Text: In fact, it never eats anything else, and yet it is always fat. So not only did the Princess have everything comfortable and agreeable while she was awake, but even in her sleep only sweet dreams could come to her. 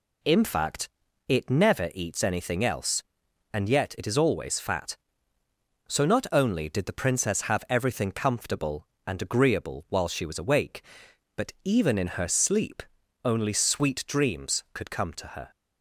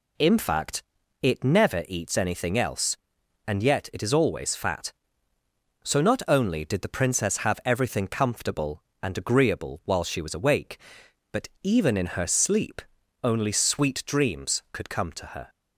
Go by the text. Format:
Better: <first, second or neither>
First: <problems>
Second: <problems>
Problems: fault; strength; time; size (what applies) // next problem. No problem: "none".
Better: neither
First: pauses between "sleep" and "only"; at 12.8 s; 0.40 s long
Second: pauses between "sleep" and "only"; at 12.8 s; 0.40 s long